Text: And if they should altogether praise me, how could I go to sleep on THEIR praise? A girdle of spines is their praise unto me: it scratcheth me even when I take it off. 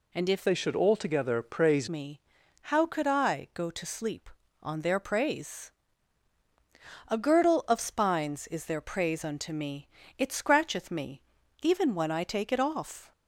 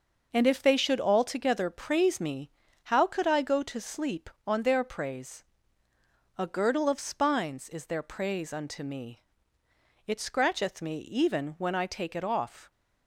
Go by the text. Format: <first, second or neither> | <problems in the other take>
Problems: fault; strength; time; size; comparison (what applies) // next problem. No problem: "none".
second | changes voice from "they" to "praise"; from 0.4 to 1.8 s; 1.4 s long // pauses between "me" and "even"; at 11.1 s; 0.44 s long